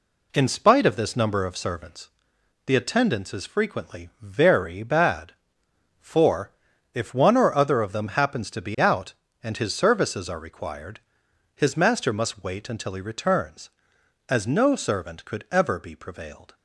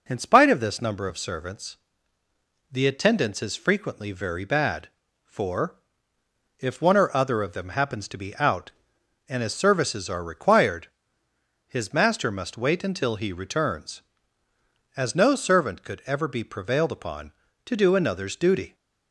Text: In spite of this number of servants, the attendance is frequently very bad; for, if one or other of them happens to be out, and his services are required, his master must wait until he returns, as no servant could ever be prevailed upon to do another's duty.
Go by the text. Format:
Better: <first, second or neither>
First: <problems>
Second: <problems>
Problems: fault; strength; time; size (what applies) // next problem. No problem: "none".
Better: second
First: stops before "upon to do another's duty"; at 16.5 s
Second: none